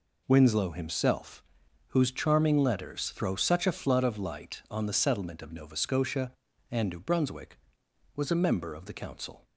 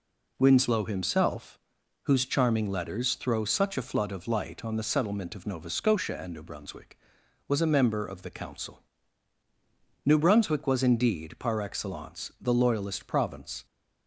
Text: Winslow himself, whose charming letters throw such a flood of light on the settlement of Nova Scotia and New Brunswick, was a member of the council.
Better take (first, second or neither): first